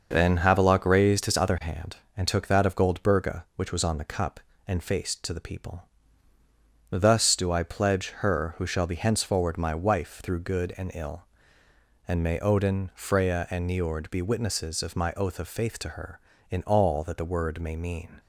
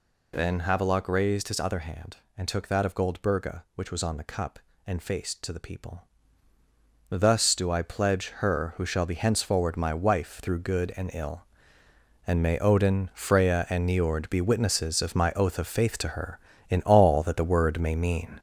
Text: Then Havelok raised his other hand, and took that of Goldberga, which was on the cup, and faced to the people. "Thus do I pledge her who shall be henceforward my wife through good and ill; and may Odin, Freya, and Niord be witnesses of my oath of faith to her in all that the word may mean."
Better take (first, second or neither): first